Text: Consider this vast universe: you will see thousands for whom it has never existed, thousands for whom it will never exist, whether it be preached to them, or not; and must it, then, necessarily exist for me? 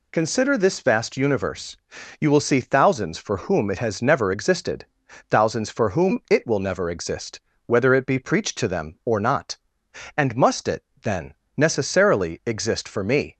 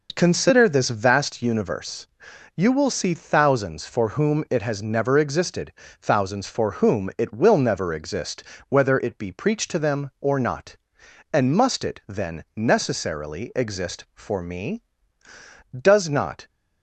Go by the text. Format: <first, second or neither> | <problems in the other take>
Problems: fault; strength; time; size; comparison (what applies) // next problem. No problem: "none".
first | goes on to say "Does not"; noticeable; from 15.7 s on; 0.70 s long